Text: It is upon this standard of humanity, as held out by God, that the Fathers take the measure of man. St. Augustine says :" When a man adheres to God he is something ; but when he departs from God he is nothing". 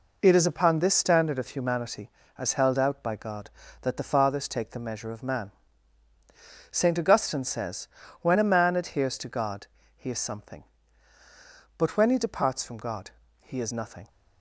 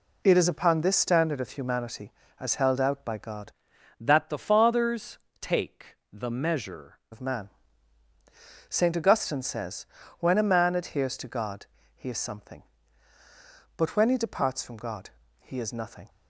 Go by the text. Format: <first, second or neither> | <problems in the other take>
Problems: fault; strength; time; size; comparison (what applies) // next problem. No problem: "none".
first | changes voice from "that" to "measure"; from 4.0 to 6.9 s; 2.9 s long // pauses between "Fathers" and "take"; slight; at 5.1 s; 0.22 s long // pauses between "take" and "the"; slight; at 5.9 s; 0.16 s long // pauses between "God" and "he"; slight; at 11.6 s; 0.28 s long; slight in the first // pauses between "God" and "he"; slight; at 15.1 s; 0.28 s long; slight in the first